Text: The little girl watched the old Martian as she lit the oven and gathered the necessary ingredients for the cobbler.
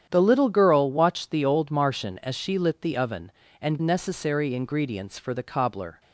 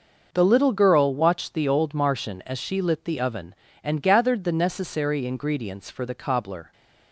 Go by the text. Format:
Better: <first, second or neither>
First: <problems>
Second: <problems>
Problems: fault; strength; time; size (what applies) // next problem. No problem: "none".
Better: second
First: starts louder than the rest; strong; until 1.1 s; 9 dB // skips "gathered the"; at 3.7 s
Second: none